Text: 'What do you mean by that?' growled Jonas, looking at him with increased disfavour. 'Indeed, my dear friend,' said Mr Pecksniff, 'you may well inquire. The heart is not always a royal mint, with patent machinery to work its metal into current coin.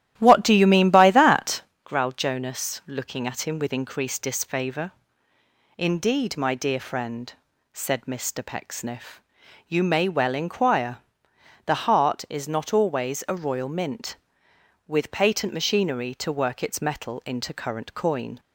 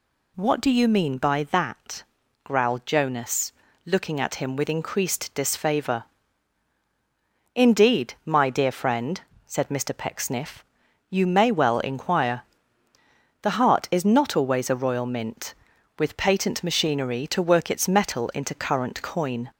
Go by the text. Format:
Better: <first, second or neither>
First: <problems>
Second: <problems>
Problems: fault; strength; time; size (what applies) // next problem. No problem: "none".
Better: second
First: starts louder than the rest; strong; until 1.8 s; 12.5 dB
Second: none